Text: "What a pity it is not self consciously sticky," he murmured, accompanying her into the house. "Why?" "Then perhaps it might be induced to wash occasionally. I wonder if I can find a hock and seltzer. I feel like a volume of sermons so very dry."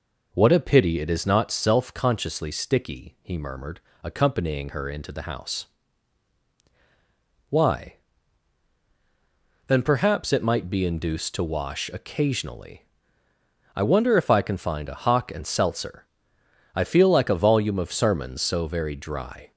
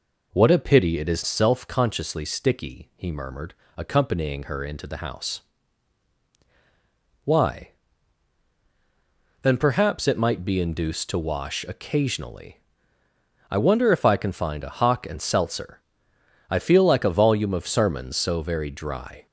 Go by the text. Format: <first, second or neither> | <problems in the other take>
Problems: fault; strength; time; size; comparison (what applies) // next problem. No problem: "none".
first | skips "not"; at 1.2 s